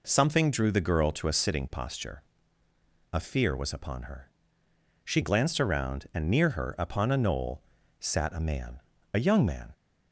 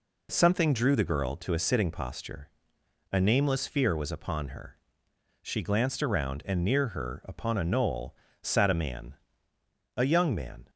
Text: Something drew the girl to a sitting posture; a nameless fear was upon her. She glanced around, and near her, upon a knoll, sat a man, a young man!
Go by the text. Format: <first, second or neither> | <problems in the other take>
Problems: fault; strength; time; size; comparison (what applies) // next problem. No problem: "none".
second | skips "nameless"; at 3.1 s